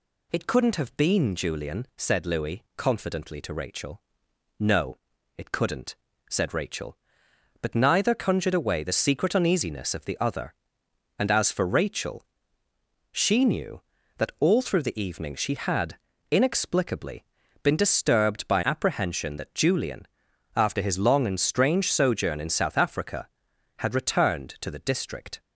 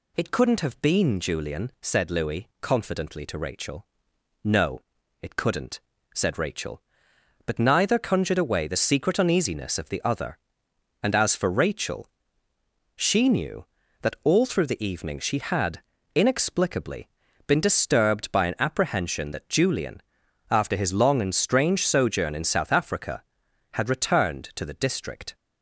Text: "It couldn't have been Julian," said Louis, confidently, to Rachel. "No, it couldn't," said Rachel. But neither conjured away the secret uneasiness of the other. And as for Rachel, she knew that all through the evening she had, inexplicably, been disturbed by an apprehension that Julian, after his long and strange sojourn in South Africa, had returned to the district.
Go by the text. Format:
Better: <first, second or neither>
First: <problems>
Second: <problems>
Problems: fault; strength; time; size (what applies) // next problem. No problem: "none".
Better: second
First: skips "an"; at 18.6 s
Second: none